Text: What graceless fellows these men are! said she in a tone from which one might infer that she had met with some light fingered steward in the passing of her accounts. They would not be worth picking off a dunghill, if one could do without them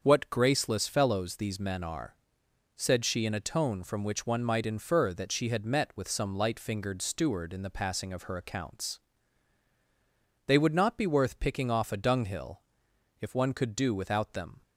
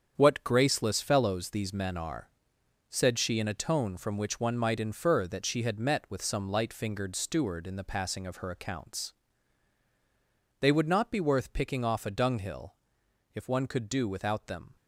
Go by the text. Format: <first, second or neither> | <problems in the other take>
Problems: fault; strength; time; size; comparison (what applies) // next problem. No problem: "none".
first | gets quieter; strong; throughout; 8.5 dB // starts louder than the rest; strong; until 1.2 s; 8 dB; also in the first